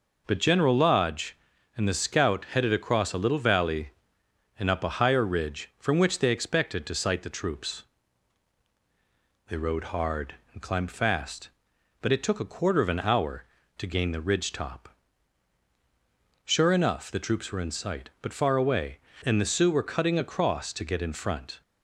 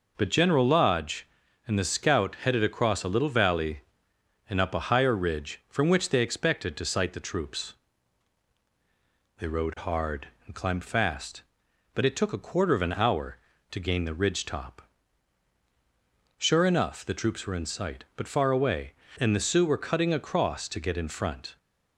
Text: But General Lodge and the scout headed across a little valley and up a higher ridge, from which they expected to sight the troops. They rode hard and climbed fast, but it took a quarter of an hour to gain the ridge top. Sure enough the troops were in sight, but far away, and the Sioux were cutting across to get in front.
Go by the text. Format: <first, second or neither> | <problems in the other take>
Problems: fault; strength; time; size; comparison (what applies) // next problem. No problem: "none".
neither | none